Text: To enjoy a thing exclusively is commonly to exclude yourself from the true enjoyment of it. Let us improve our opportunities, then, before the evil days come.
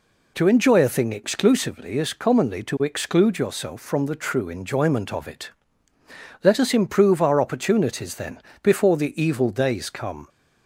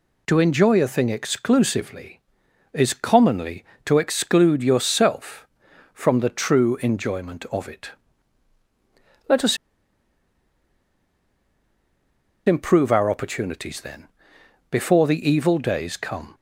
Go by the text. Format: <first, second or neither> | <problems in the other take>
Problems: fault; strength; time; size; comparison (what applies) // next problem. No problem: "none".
first | pauses between "us" and "improve"; strong; at 9.5 s; 2.8 s long